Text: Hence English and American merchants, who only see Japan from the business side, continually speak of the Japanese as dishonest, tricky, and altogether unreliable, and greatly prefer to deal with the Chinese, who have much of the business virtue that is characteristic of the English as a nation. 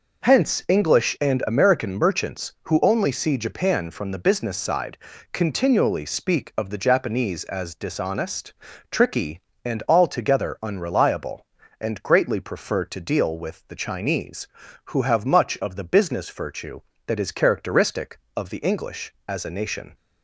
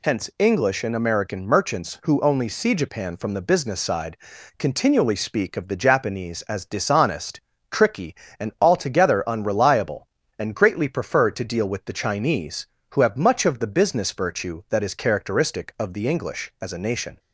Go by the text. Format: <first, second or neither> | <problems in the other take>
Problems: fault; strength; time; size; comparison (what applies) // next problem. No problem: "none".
neither | none